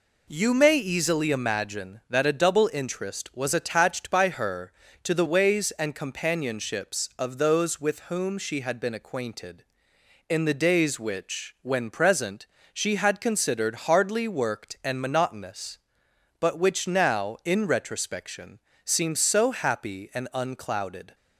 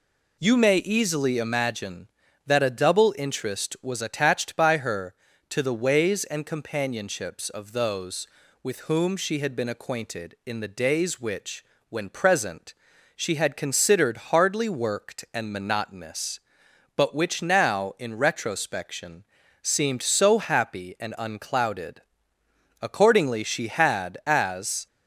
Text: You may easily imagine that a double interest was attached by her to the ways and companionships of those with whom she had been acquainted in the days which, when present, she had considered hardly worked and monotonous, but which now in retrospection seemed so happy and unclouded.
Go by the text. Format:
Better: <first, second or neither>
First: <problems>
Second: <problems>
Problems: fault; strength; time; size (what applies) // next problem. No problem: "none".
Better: first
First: pauses between "retrospection" and "seemed"; slight; at 18.5 s; 0.24 s long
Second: pauses between "retrospection" and "seemed"; at 19.2 s; 0.38 s long // goes on to say "Accordingly she had as"; strong; from 22.8 s on; 2.0 s long